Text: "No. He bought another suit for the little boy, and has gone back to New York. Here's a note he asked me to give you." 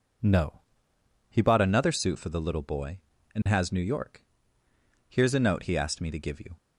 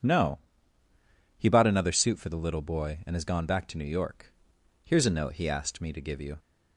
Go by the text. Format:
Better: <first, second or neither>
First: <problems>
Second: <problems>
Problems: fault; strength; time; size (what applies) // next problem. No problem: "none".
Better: second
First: skips "gone back to"; at 3.7 s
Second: none